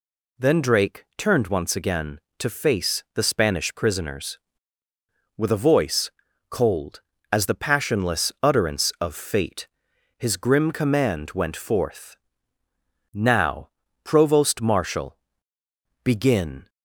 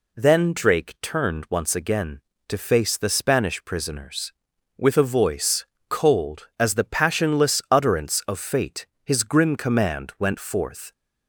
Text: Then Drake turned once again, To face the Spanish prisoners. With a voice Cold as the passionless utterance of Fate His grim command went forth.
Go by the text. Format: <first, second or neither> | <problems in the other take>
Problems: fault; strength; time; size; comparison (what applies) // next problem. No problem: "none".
second | pauses between "voice" and "Cold"; at 6.1 s; 0.38 s long; slight in the second // pauses between "Fate" and "His"; noticeable; at 9.6 s; 0.52 s long; slight in the second // goes on to say "Now provost marshal Begin"; strong; from 13.1 s on; 3.5 s long